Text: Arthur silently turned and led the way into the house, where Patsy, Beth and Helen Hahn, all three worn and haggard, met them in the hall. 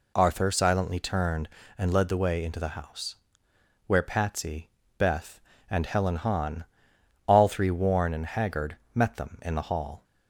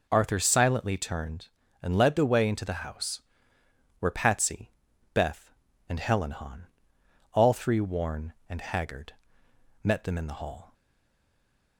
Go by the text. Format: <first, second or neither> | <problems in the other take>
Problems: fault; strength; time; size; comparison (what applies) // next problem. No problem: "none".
first | stays silent after the last word; from 10.7 s on; 1.0 s long